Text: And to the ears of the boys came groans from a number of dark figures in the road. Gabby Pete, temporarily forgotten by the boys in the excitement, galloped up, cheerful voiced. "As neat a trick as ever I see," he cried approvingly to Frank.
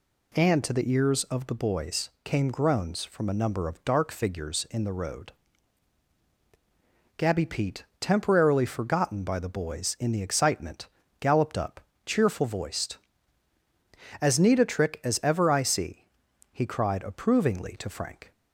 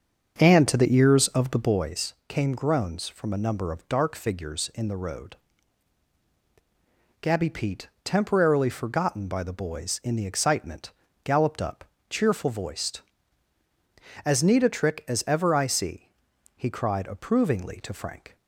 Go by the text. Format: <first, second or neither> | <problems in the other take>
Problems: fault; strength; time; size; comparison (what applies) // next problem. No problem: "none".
first | starts louder than the rest; until 1.9 s; 7 dB // pauses between "boys" and "came"; slight; at 2.1 s; 0.16 s long; slight in the first